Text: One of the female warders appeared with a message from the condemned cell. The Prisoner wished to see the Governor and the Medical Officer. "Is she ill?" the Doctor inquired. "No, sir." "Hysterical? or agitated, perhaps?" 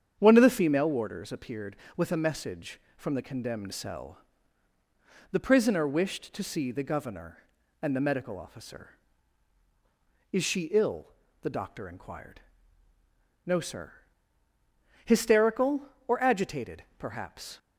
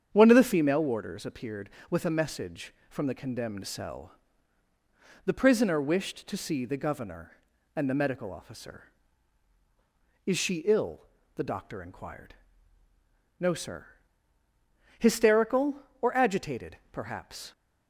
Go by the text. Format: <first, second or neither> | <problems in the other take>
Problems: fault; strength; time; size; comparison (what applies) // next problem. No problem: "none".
neither | starts louder than the rest; strong; the same in both